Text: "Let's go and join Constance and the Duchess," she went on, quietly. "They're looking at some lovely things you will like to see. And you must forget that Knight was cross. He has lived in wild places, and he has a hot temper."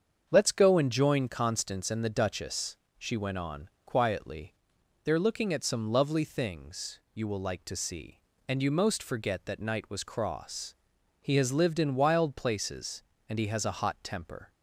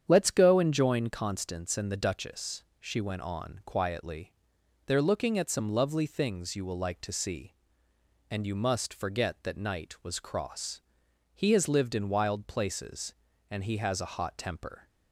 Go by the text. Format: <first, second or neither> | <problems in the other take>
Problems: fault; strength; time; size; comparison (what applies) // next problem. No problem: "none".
second | starts louder than the rest; strong; until 1.3 s; 7.5 dB; strong in the second // says "most" for "must"; at 8.6 s